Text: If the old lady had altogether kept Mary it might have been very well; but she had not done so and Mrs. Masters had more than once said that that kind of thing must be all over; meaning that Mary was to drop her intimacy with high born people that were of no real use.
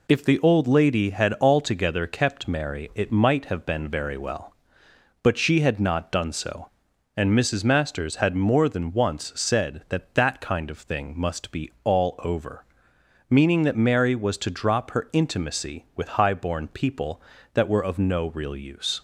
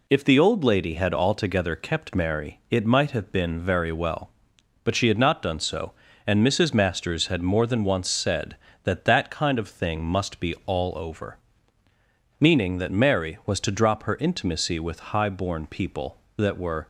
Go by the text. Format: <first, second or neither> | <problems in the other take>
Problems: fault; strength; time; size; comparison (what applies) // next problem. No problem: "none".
first | stops before "of no real use"; at 16.8 s